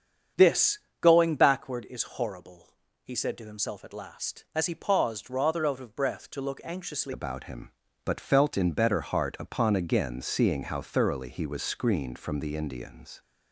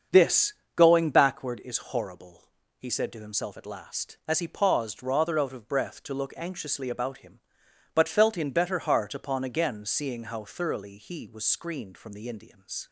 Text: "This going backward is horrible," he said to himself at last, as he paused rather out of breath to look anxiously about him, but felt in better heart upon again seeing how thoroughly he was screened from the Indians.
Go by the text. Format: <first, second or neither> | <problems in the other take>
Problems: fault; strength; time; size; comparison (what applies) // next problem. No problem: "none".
second | starts louder than the rest; strong; until 1.5 s; 8 dB; also in the second // pauses between "This" and "going"; slight; at 0.8 s; 0.20 s long; slight in the second // changes voice at "about"; from 7.1 s on; 6.1 s long